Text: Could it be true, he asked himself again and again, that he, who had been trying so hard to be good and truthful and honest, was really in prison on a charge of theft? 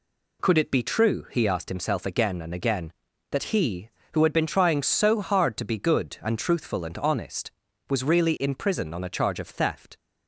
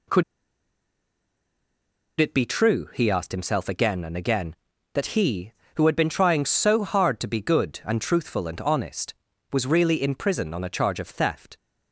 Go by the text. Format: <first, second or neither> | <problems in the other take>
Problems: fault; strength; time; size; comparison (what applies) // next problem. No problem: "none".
first | pauses between "Could" and "it"; strong; at 0.2 s; 1.9 s long